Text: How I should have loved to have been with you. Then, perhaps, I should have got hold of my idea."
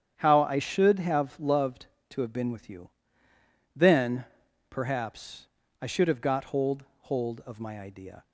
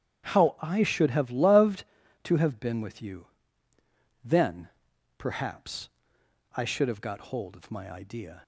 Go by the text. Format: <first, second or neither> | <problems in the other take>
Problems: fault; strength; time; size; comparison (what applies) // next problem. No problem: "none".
second | starts louder than the rest; strong; until 1.1 s; 9 dB; strong in the second // says "hold" twice; at 7.0 s